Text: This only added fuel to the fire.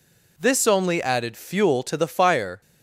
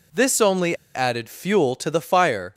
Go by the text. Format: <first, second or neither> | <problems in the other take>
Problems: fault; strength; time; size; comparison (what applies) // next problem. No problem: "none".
first | pauses between "only" and "added"; slight; at 0.7 s; 0.18 s long